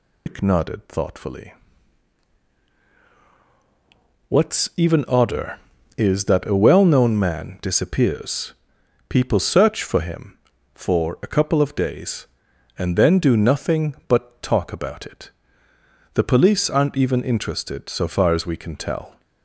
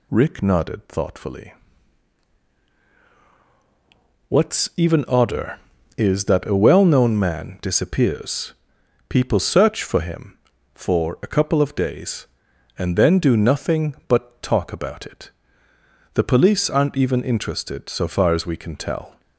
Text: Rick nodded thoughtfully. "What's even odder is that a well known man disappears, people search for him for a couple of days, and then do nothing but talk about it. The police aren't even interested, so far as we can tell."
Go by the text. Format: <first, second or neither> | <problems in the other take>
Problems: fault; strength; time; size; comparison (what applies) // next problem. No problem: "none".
second | loses the start of "Rick"; at 0.2 s; 160 ms